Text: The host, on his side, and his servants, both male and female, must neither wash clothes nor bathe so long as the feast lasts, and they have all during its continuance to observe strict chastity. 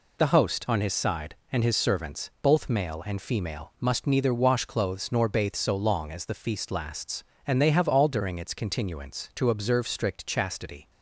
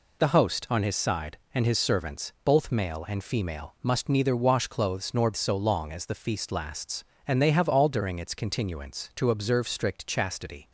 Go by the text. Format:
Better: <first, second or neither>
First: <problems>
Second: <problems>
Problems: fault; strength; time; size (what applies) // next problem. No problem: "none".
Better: first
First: none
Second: skips "bathe"; at 5.3 s